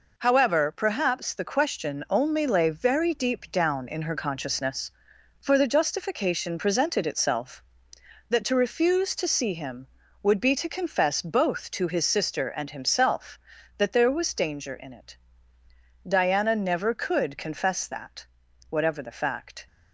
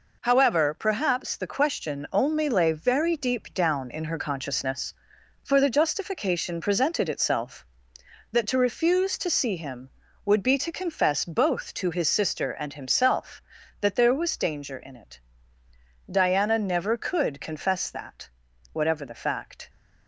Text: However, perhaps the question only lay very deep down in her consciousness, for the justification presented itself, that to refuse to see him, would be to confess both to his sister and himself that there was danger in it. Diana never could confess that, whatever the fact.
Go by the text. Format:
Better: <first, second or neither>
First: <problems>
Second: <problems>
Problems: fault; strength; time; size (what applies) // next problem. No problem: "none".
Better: neither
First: none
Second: none